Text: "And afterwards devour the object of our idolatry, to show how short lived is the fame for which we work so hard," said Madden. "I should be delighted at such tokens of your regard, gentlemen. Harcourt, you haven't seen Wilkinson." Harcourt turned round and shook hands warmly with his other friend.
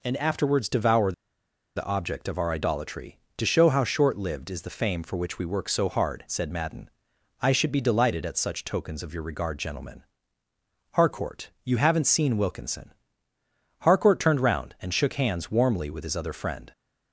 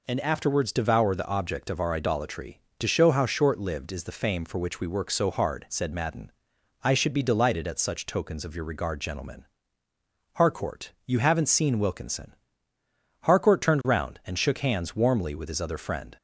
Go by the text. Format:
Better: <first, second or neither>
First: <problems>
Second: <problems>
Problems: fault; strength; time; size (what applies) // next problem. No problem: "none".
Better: second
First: pauses between "devour" and "the"; noticeable; at 1.1 s; 0.63 s long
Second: none